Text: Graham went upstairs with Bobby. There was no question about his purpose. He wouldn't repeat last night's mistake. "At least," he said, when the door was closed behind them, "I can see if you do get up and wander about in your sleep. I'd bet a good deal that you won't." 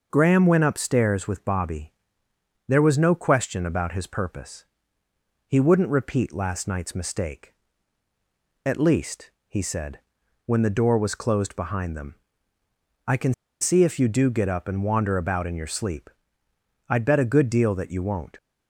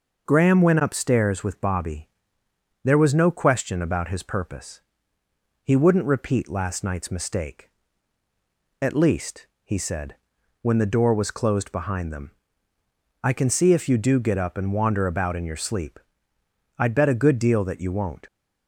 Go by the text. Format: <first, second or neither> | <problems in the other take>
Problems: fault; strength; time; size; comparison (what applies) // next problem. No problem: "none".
second | pauses between "can" and "see"; slight; at 13.3 s; 0.28 s long